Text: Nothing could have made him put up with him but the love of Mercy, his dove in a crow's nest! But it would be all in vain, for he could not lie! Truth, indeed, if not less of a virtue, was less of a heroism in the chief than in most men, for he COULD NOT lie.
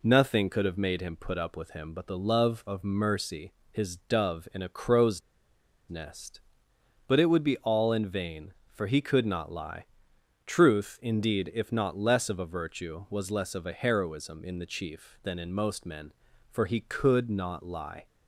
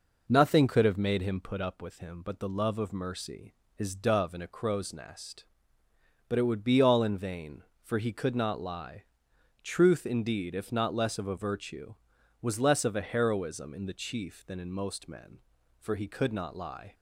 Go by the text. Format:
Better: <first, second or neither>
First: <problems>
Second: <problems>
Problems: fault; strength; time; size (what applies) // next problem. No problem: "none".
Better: second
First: pauses between "crow's" and "nest"; noticeable; at 5.2 s; 0.69 s long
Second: none